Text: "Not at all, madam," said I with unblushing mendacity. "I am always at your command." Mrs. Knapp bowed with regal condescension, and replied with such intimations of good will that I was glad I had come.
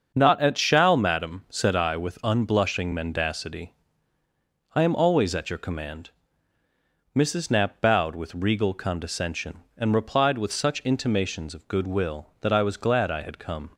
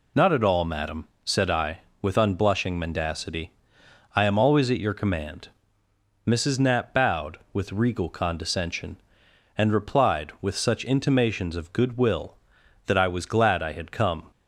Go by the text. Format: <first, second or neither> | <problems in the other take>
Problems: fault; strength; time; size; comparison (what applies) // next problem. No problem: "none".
second | starts louder than the rest; until 1.1 s; 7 dB // says "shall" for "all"; at 0.5 s